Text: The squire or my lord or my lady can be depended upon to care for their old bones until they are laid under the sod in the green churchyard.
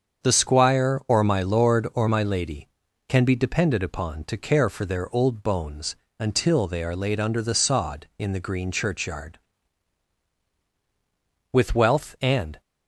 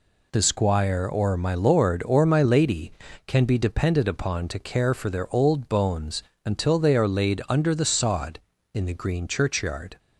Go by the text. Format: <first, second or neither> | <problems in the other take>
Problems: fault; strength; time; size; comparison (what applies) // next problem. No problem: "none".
second | starts louder than the rest; strong; until 1.3 s; 7 dB // pauses between "bones" and "until"; slight; at 5.9 s; 0.24 s long; slight in the second // goes on to say "With wealth and"; noticeable; from 11.5 s on; 1.0 s long